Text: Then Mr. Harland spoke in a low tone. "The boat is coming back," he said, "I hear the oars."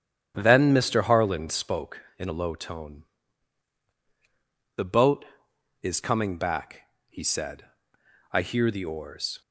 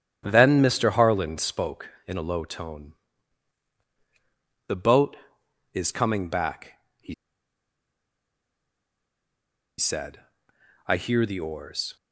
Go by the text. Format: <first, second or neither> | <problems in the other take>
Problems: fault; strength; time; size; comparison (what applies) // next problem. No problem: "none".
first | starts louder than the rest; strong; until 1.2 s; 9.5 dB; strong in the first // pauses between "he" and "said"; strong; at 7.1 s; 2.6 s long